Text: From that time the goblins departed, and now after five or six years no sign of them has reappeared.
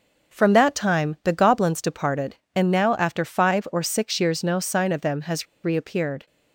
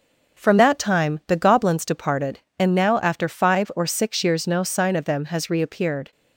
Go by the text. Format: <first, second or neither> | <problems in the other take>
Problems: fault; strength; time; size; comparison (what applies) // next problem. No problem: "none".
second | starts louder than the rest; noticeable; until 1.3 s; 6 dB; also in the second // pauses between "has" and "reappeared"; slight; at 5.4 s; 0.17 s long